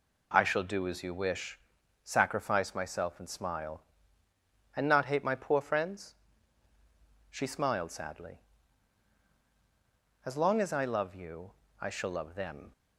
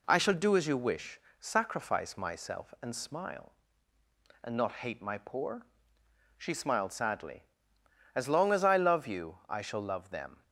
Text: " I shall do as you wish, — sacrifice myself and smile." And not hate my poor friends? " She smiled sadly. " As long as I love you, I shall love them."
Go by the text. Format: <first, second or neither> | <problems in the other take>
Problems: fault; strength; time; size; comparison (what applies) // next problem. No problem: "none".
first | skips "friends"; at 5.8 s